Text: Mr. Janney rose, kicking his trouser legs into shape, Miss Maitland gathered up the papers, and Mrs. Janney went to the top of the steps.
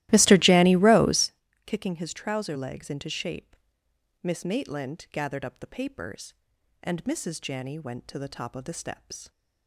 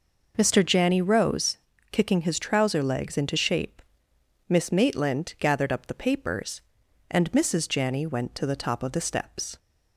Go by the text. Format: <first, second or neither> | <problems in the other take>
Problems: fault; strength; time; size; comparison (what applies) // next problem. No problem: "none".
second | starts louder than the rest; strong; until 1.4 s; 16.5 dB